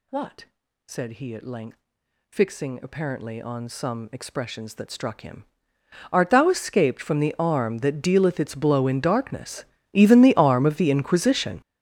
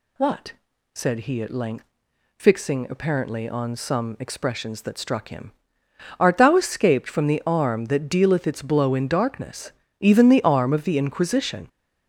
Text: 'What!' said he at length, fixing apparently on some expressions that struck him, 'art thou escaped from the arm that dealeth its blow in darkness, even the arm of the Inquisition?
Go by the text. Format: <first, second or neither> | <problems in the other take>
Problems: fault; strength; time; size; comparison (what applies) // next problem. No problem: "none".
second | gets louder; strong; throughout; 16 dB